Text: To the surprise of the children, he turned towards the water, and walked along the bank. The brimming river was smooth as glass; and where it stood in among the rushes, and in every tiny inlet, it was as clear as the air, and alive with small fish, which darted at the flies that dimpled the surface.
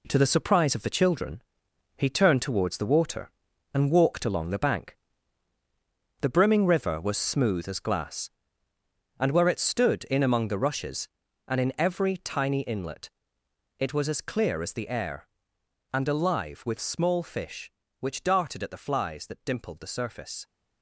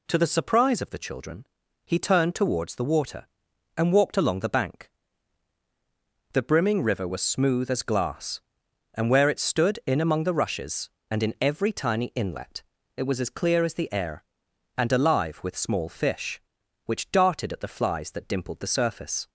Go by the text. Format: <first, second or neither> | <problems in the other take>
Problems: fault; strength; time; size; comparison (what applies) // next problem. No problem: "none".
second | gets quieter; strong; throughout; 8.5 dB